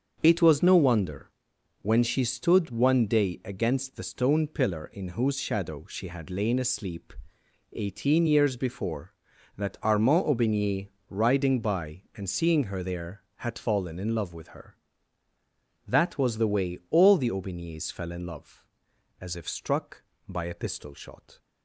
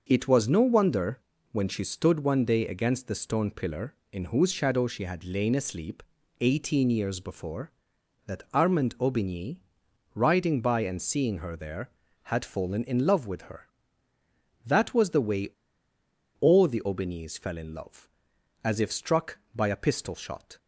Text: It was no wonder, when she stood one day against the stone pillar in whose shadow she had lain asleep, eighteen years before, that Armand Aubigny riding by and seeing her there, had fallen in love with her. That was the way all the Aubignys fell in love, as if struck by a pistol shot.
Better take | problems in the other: first | starts louder than the rest; noticeable; until 1.0 s; 6 dB; also in the first // pauses between "Aubigny" and "riding"; noticeable; at 9.5 s; 0.58 s long; slight in the first // pauses between "way" and "all"; noticeable; at 15.4 s; 0.90 s long

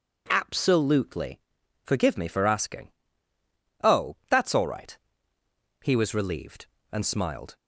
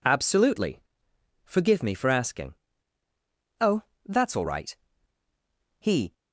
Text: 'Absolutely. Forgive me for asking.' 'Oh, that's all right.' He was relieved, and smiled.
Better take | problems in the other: first | stops before "was relieved and smiled"; at 6.1 s

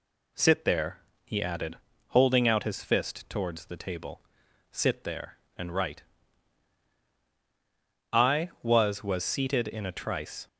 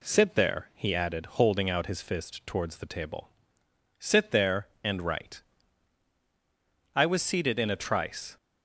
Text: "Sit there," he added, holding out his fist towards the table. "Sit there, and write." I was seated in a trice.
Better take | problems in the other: second | says "was" twice; at 9.0 s

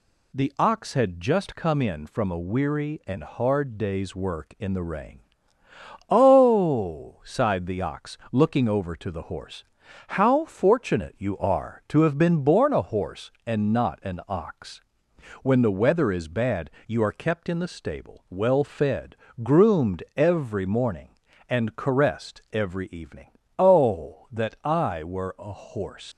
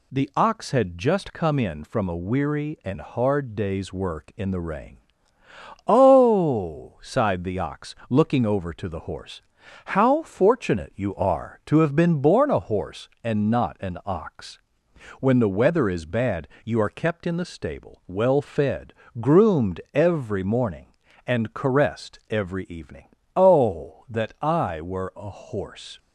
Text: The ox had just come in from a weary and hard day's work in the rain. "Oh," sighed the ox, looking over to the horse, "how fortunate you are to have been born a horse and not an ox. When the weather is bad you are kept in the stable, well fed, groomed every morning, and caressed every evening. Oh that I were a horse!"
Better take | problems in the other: second | pauses between "bad" and "you"; slight; at 16.6 s; 0.18 s long; slight in the second // leaves "horse" unfinished; at 26.1 s; 85 ms

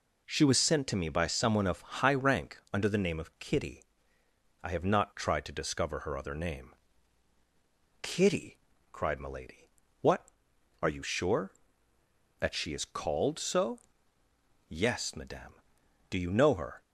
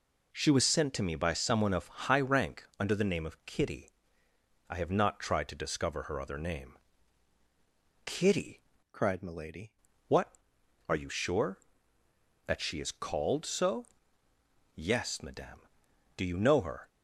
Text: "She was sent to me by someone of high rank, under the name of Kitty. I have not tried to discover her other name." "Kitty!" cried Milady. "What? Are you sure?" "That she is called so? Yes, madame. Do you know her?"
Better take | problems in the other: first | changes voice from "cried" to "Milady"; from 8.9 to 9.7 s; 0.8 s long

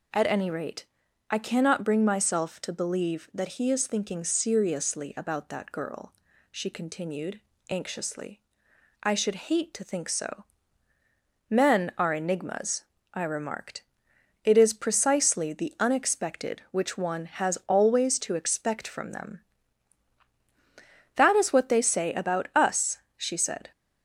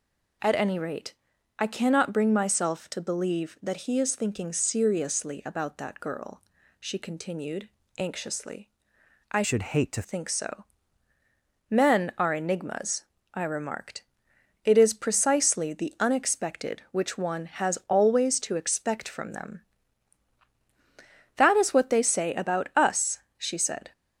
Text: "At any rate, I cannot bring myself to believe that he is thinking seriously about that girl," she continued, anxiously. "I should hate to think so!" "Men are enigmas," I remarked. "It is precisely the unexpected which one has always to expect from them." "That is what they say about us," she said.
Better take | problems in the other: first | changes voice from "should" to "to"; from 9.4 to 10.0 s; 0.6 s long

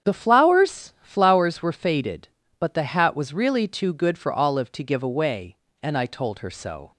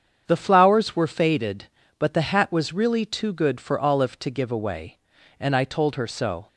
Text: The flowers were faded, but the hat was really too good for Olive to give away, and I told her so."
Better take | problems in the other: second | starts louder than the rest; strong; until 1.1 s; 8 dB; strong in the second // says "flowers" twice; at 1.0 s

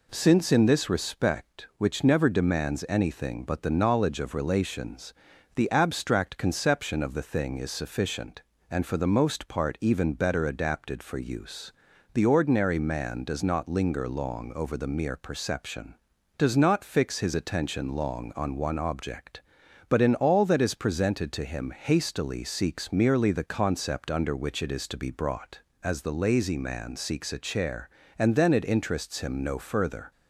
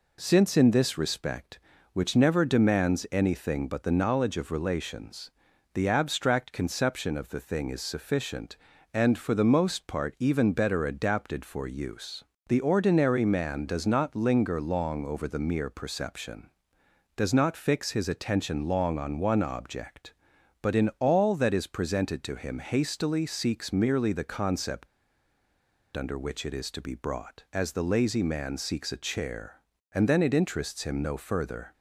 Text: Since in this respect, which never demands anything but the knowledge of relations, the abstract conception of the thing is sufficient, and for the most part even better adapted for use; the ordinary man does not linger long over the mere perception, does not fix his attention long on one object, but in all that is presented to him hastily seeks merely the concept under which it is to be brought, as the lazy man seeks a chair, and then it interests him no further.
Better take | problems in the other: first | pauses between "concept" and "under"; at 24.8 s; 1.1 s long

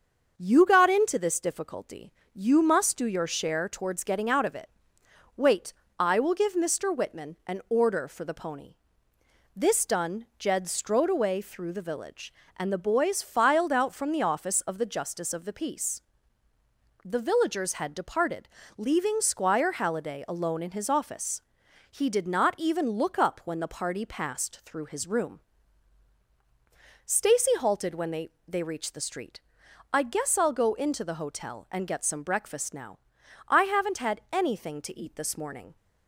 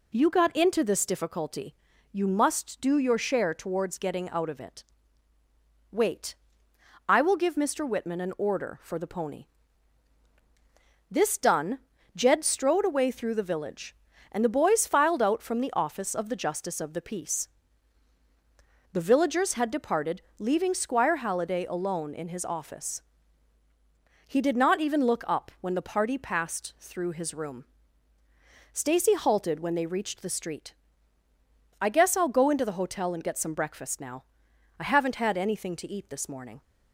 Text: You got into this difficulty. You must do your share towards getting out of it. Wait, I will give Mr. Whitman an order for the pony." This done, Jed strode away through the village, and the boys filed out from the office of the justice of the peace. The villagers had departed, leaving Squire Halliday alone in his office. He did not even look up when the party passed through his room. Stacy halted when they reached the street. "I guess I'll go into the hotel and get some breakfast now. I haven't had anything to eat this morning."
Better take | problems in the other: second | starts louder than the rest; until 1.3 s; 6.5 dB // says "they" twice; at 28.4 s

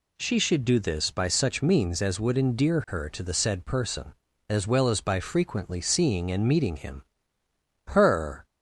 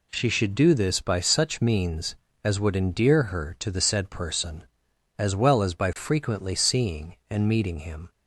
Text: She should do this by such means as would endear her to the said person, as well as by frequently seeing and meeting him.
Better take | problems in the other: second | goes on to say "Her"; from 7.8 s on; 0.56 s long

